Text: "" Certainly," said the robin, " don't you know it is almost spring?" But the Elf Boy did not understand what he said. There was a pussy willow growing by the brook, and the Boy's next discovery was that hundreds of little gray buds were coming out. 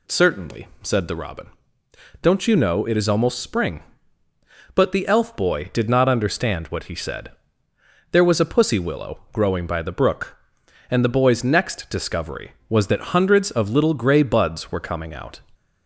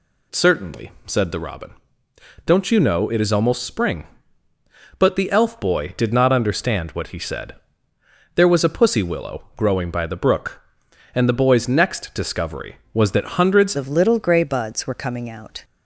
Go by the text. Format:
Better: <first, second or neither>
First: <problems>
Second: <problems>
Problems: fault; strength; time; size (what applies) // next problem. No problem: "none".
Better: first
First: none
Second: changes voice at "of"; from 13.7 s on; 1.9 s long